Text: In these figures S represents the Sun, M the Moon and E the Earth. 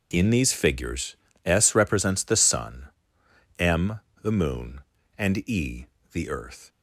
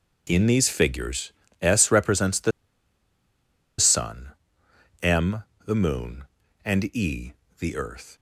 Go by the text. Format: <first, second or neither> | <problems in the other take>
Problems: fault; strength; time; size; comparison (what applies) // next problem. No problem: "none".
first | pauses between "figures" and "S"; slight; at 1.3 s; 0.30 s long; slight in the first // pauses between "the" and "Sun"; strong; at 2.5 s; 1.2 s long // pauses between "M" and "the"; slight; at 5.4 s; 0.22 s long; slight in the first // pauses between "E" and "the"; slight; at 7.3 s; 0.28 s long; slight in the first